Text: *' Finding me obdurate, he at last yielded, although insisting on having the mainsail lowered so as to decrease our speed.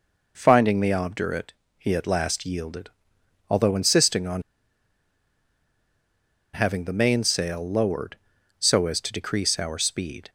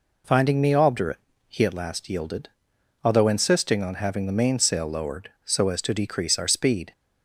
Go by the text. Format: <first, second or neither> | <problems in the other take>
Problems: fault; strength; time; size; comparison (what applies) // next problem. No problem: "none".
second | pauses between "on" and "having"; strong; at 4.4 s; 2.1 s long